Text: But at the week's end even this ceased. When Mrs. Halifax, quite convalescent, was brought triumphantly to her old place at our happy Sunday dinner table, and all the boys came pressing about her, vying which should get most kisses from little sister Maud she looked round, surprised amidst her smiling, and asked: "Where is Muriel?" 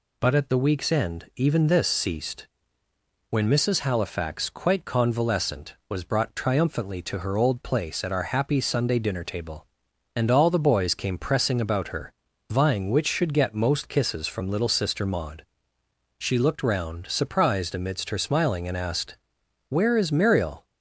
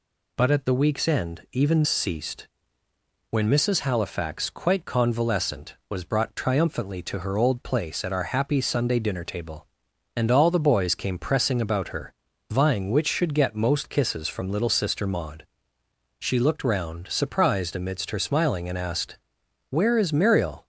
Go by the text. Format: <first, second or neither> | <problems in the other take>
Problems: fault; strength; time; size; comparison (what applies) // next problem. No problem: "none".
first | skips "this"; at 1.8 s // pauses between "Maud" and "she"; noticeable; at 15.4 s; 0.76 s long; noticeable in the first